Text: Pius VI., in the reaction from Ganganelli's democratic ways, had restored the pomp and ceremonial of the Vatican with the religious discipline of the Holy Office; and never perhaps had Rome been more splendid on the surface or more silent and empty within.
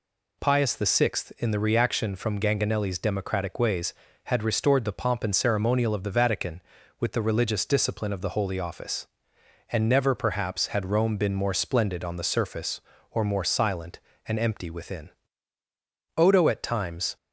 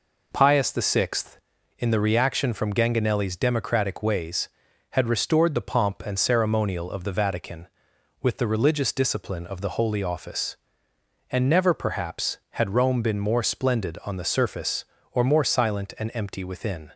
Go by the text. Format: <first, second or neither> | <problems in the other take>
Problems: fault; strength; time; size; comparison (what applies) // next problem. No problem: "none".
second | goes on to say "Odo at times"; noticeable; from 16.1 s on; 0.98 s long